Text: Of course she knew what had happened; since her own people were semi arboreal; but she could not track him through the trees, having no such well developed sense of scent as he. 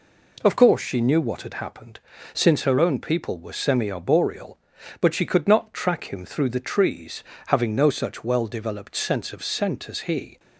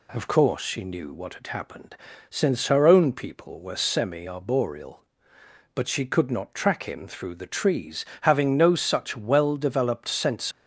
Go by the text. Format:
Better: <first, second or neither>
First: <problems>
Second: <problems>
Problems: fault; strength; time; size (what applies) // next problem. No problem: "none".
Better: first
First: none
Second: stops before "of scent as he"; at 10.5 s